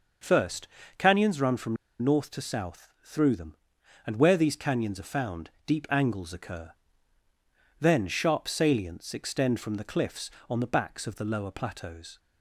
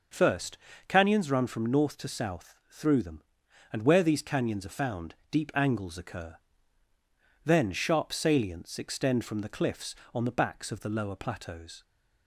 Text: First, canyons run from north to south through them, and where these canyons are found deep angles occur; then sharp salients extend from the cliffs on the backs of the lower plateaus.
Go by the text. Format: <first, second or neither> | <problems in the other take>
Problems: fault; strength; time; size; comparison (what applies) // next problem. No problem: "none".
second | pauses between "from" and "north"; slight; at 1.7 s; 0.25 s long // pauses between "found" and "deep"; slight; at 5.4 s; 0.16 s long; slight in the second